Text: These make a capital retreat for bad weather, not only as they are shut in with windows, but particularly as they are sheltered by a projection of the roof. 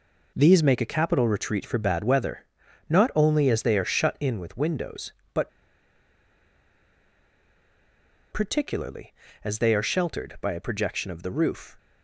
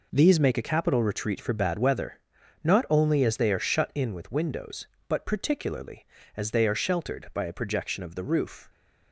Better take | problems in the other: second | pauses between "but" and "particularly"; strong; at 5.4 s; 2.8 s long

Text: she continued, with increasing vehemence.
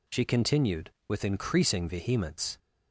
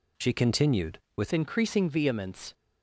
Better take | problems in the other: first | changes voice at "increasing"; from 1.3 s on; 1.2 s long

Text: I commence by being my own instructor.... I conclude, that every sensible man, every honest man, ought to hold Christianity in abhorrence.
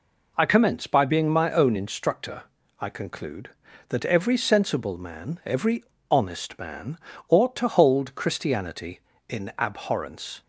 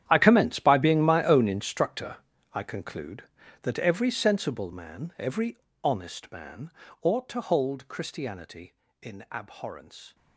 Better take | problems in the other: first | gets quieter; strong; throughout; 17.5 dB // pauses between "every" and "honest"; slight; at 5.5 s; 0.26 s long; slight in the first

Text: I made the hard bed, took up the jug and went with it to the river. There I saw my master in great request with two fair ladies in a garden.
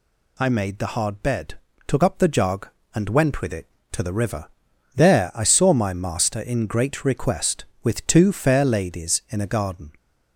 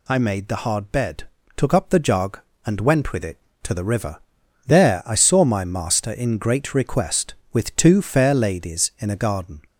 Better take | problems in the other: neither | none

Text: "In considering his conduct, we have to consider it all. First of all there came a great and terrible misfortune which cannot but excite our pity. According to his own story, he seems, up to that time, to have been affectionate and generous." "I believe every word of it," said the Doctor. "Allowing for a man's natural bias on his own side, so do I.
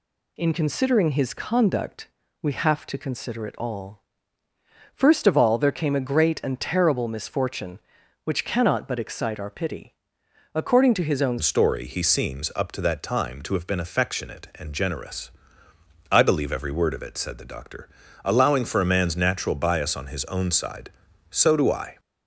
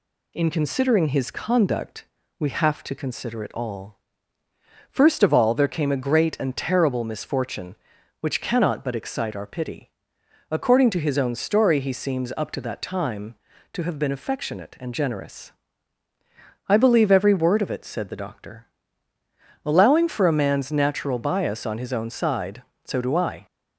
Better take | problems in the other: second | changes voice at "story"; from 11.4 s on; 10.5 s long

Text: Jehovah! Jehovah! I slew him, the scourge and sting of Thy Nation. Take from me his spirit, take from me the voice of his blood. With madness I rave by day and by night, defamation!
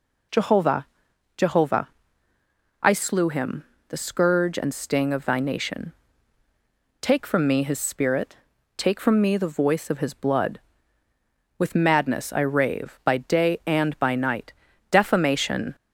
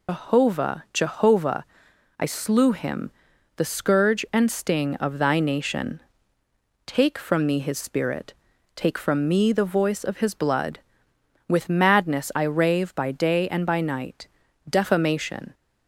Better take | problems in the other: first | loses the start of "Jehovah"; at 0.0 s; 130 ms

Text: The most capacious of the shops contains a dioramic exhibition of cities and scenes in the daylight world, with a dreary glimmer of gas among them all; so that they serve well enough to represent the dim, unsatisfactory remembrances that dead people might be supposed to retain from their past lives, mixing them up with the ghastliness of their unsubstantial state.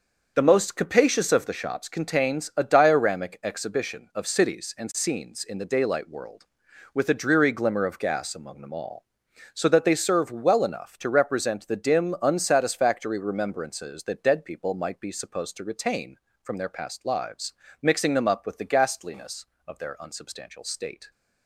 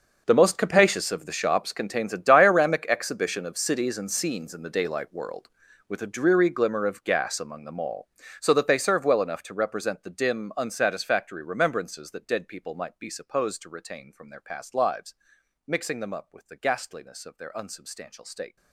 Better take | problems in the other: first | gets quieter; strong; throughout; 18 dB // starts louder than the rest; until 1.2 s; 6 dB; also in the first

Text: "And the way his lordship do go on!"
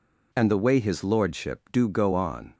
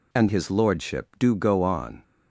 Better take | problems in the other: first | skips "the way"; at 0.2 s

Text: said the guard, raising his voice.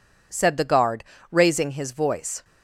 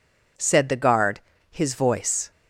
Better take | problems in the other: first | skips "raising"; at 1.3 s

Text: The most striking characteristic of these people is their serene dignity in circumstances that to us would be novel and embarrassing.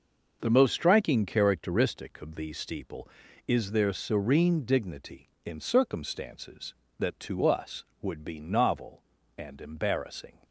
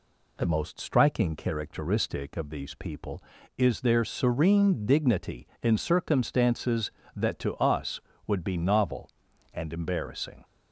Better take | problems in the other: second | starts louder than the rest; noticeable; until 1.4 s; 6 dB // says "steeple" for "people"; at 2.5 s

